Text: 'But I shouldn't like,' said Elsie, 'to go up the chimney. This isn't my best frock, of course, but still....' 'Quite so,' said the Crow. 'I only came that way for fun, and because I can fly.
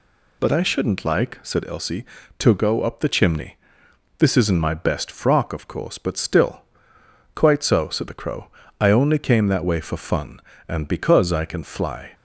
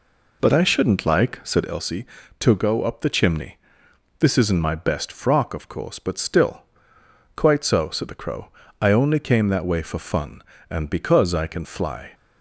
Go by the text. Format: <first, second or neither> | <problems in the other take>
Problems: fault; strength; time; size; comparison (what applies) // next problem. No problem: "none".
first | starts louder than the rest; until 1.9 s; 3.5 dB